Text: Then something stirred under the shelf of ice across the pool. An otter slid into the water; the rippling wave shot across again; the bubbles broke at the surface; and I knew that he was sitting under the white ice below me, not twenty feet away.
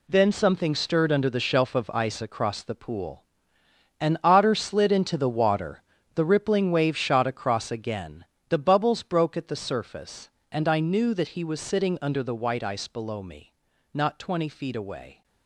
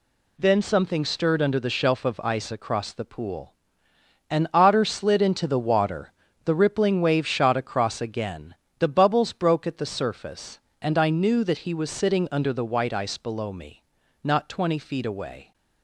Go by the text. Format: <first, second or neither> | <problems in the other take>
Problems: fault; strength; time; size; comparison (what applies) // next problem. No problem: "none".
second | gets quieter; strong; throughout; 9.5 dB